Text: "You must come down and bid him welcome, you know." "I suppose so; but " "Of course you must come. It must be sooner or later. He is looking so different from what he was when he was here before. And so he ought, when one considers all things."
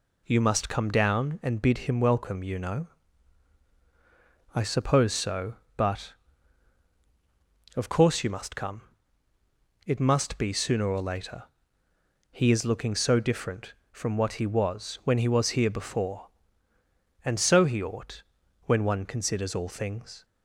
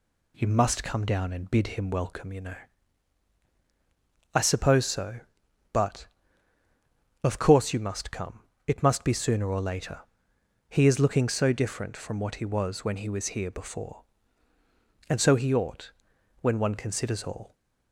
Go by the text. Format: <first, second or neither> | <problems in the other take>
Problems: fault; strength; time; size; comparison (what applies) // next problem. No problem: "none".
first | stops before "things"; at 17.5 s